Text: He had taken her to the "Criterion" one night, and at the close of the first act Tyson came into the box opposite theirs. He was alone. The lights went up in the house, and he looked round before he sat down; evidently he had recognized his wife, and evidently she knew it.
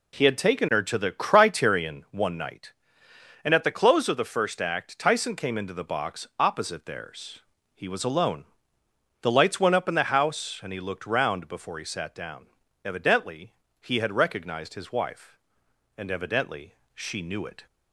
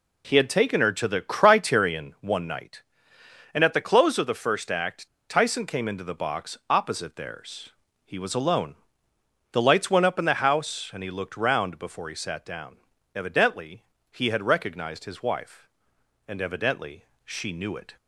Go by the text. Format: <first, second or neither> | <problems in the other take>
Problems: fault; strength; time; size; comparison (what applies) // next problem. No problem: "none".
first | pauses between "act" and "Tyson"; slight; at 5.0 s; 0.21 s long // pauses between "evidently" and "he"; slight; at 13.8 s; 0.30 s long; slight in the first // pauses between "evidently" and "she"; slight; at 17.0 s; 0.18 s long; slight in the first